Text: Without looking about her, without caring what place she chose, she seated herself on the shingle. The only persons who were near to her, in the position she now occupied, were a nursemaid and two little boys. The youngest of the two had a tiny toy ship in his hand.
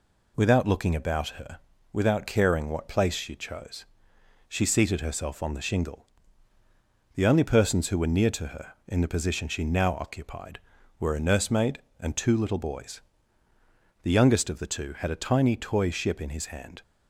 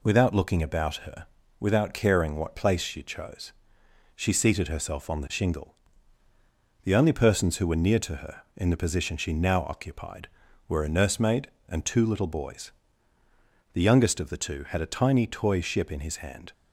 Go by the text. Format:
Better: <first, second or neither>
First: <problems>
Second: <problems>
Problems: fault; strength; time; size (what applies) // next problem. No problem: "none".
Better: neither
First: none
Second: none